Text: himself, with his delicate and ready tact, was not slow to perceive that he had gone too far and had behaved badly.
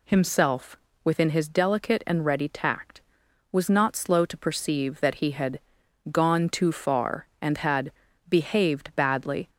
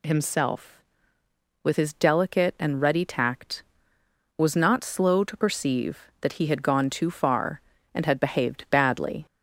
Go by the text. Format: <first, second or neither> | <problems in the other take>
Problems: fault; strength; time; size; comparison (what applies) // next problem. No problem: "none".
second | says "within" for "with"; at 1.0 s // pauses between "had" and "gone"; noticeable; at 5.5 s; 0.52 s long // pauses between "had" and "behaved"; at 7.9 s; 0.38 s long